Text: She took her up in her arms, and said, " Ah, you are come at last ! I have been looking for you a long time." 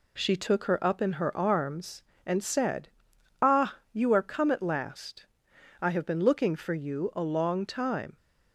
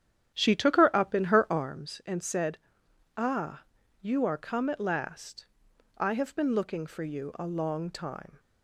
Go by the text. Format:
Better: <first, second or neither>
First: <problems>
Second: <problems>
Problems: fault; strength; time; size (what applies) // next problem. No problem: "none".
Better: first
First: none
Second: starts louder than the rest; strong; until 1.7 s; 9.5 dB